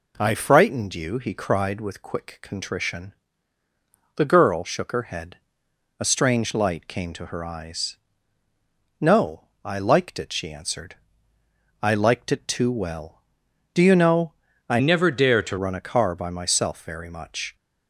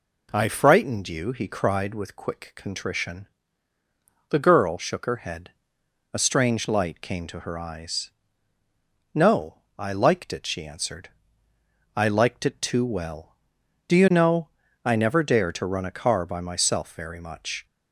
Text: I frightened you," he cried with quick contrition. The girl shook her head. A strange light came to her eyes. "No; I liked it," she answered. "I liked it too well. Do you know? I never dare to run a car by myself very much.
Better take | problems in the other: second | changes voice from "never" to "to"; from 14.7 to 15.5 s; 0.8 s long

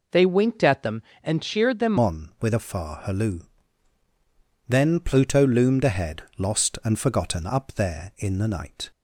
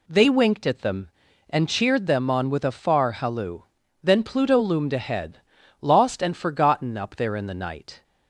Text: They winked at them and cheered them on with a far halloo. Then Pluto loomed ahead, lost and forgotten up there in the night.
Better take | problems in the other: second | changes voice at "on"; from 1.9 s on; 7.0 s long

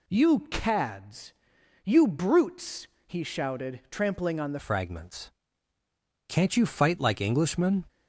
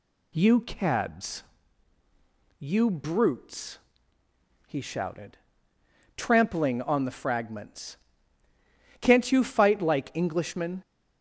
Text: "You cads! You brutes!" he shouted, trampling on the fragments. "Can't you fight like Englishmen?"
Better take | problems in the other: second | changes voice at "fragments"; from 4.5 s on; 3.3 s long

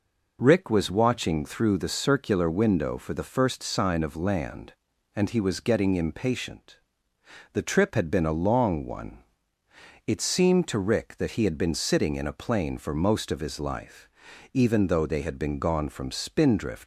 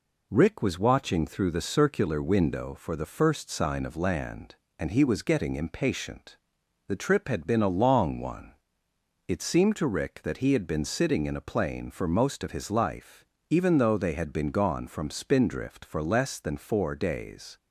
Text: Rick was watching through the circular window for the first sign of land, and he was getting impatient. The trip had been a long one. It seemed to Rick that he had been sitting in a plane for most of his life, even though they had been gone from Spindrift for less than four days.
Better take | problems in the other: second | stops before "for less than four days"; at 16.8 s

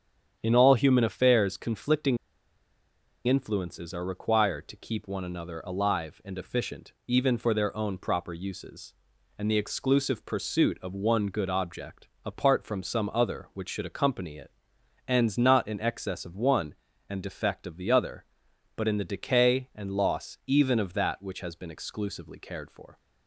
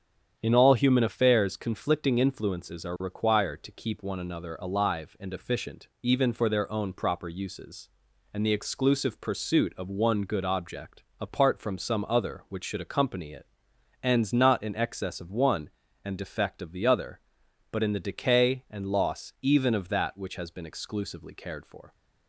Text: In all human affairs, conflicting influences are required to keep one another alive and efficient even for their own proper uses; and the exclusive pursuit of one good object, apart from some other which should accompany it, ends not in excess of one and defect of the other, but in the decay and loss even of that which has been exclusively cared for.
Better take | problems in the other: second | starts louder than the rest; strong; until 1.4 s; 8.5 dB; strong in the second // pauses between "conflicting" and "influences"; at 2.1 s; 1.1 s long

